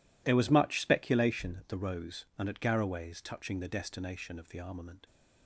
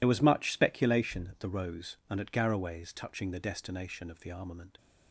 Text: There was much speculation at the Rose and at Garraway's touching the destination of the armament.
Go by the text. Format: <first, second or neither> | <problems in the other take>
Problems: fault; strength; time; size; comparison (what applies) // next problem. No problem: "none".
first | loses the start of "There"; at 0.0 s; 60 ms